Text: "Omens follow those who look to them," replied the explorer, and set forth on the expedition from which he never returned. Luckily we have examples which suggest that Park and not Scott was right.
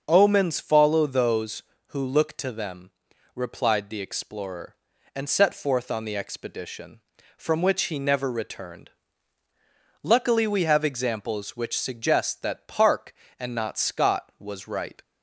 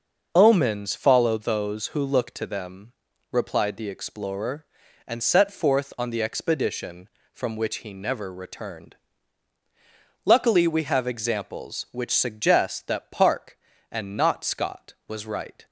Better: neither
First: starts louder than the rest; until 1.0 s; 6.5 dB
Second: starts louder than the rest; until 1.3 s; 6 dB

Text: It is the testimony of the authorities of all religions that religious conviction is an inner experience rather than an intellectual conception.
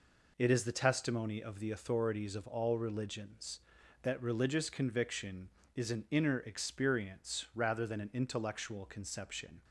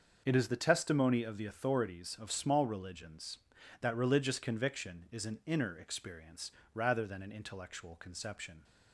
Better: first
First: none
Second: starts louder than the rest; until 1.2 s; 6.5 dB // says "small" for "all"; at 2.3 s // pauses between "experience" and "rather"; slight; at 6.5 s; 0.22 s long

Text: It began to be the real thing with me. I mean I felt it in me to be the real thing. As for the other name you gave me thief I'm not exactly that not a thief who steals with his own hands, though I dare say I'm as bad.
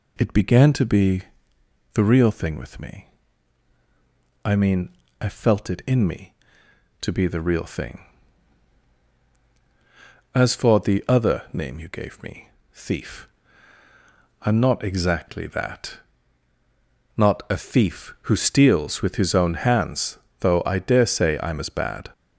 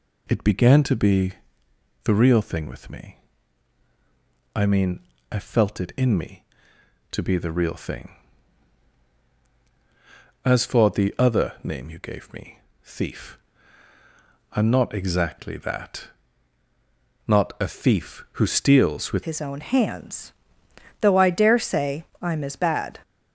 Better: first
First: pauses between "be" and "the"; noticeable; at 1.2 s; 0.70 s long // pauses between "mean" and "I"; slight; at 4.8 s; 0.32 s long // pauses between "me" and "thief"; slight; at 12.4 s; 0.26 s long // pauses between "thief" and "I'm"; at 13.2 s; 1.1 s long // pauses between "that" and "not"; at 15.9 s; 1.1 s long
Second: pauses between "be" and "the"; noticeable; at 1.3 s; 0.70 s long // pauses between "mean" and "I"; slight; at 4.9 s; 0.32 s long // pauses between "me" and "thief"; slight; at 12.5 s; 0.26 s long // pauses between "thief" and "I'm"; at 13.3 s; 1.1 s long // pauses between "that" and "not"; at 16.0 s; 1.1 s long // changes voice at "his"; from 19.2 s on; 3.7 s long // pauses between "say" and "I'm"; slight; at 22.0 s; 0.18 s long

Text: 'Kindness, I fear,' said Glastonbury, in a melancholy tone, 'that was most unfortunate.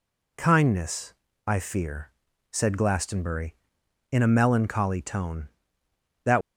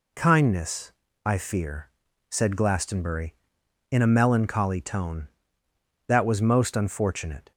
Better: second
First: stops before "was most unfortunate"; at 6.4 s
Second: none

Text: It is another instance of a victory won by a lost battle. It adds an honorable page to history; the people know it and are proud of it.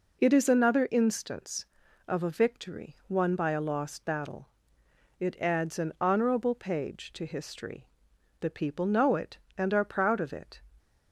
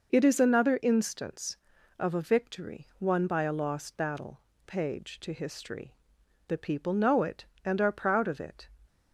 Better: first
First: none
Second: skips "It adds an honorable"; at 4.5 s

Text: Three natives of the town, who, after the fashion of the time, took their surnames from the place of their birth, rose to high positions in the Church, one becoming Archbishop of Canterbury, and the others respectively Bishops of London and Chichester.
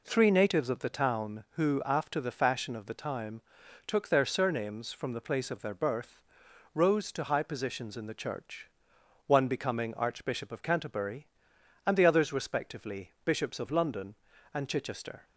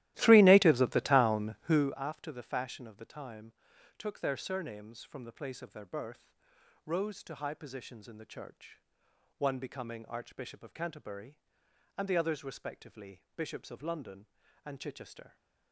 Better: first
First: none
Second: starts louder than the rest; strong; until 2.0 s; 15.5 dB

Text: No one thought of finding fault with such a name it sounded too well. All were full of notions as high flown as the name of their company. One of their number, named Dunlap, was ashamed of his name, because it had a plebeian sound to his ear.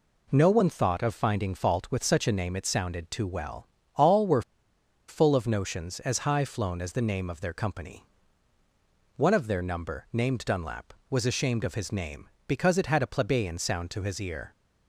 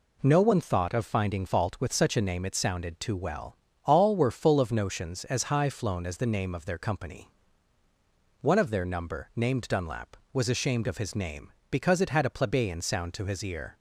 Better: second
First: pauses between "were" and "full"; noticeable; at 4.4 s; 0.66 s long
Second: none

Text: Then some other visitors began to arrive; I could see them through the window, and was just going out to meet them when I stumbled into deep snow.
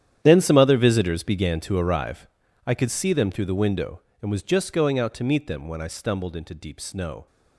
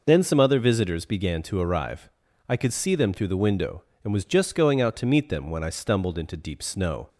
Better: second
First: gets quieter; strong; throughout; 16 dB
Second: none

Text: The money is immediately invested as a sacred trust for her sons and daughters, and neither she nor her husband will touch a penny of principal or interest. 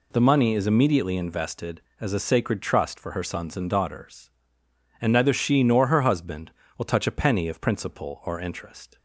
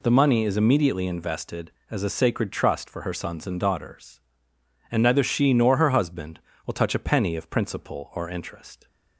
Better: neither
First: none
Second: none

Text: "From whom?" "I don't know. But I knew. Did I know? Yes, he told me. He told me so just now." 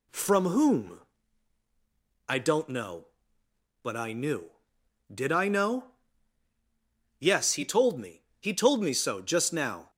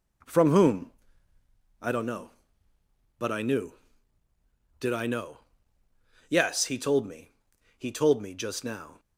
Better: first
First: none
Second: skips "so"; at 8.3 s

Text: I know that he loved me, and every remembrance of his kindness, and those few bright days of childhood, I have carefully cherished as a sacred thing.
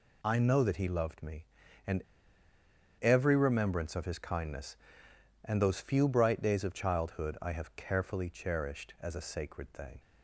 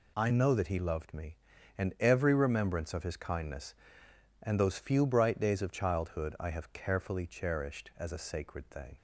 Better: second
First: pauses between "and" and "every"; at 2.0 s; 1.0 s long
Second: none

